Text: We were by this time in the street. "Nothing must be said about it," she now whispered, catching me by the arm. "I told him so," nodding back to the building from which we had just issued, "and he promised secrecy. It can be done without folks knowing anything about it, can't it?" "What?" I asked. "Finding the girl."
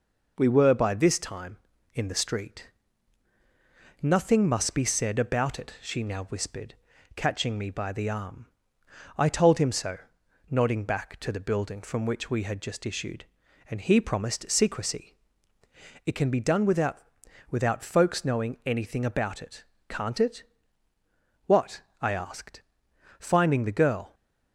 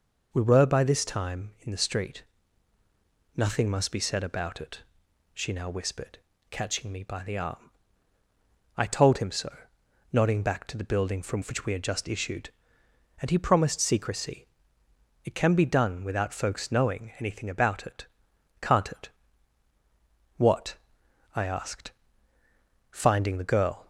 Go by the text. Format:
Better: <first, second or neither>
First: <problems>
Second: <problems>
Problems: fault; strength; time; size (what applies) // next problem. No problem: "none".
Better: second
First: says "without" twice; at 17.4 s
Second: none